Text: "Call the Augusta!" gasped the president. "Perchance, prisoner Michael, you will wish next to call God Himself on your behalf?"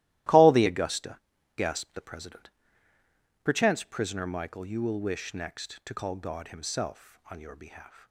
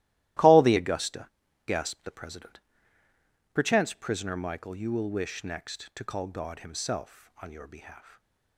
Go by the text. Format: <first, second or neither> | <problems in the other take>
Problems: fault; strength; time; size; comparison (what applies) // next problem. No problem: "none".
neither | starts louder than the rest; strong; the same in both